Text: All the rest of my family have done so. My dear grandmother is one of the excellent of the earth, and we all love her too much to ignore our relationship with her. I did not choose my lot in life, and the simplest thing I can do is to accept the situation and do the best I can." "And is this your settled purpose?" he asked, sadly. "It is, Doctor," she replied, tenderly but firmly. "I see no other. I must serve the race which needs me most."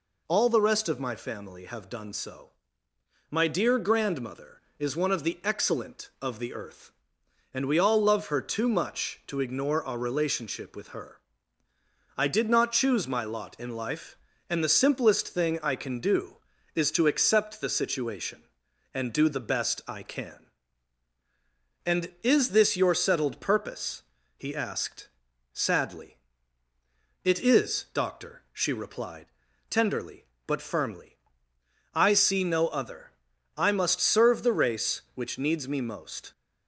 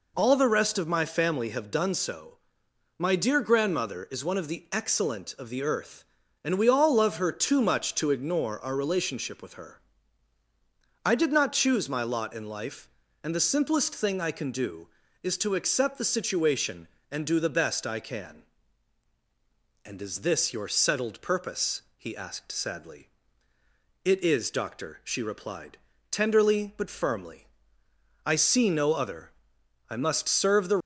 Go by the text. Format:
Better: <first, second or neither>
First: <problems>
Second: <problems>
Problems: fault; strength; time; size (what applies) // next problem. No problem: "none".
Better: first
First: none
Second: stops before "race which needs me most"; at 30.8 s